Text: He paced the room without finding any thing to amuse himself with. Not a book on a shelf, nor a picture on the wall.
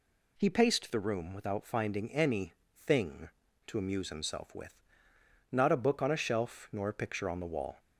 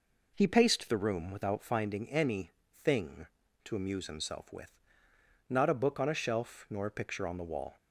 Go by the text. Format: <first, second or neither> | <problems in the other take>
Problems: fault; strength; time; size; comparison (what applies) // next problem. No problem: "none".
first | starts louder than the rest; noticeable; until 1.9 s; 4.5 dB // pauses between "any" and "thing"; slight; at 2.5 s; 0.22 s long; slight in the first